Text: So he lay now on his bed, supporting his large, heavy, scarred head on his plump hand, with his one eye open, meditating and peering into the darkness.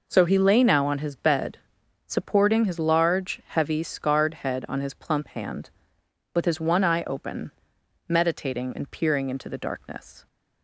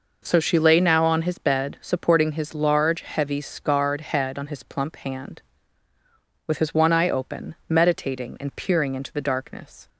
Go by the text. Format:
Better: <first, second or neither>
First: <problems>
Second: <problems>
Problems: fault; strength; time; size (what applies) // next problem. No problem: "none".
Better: first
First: none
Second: says "she" for "he"; at 0.3 s